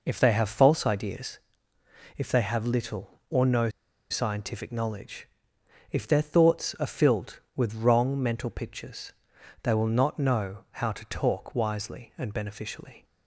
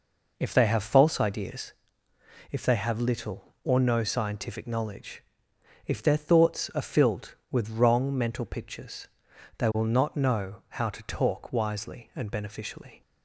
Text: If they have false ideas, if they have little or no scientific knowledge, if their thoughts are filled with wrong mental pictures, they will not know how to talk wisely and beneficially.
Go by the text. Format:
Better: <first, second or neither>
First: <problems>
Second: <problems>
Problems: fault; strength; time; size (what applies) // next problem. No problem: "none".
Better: second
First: pauses between "no" and "scientific"; at 3.6 s; 0.41 s long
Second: none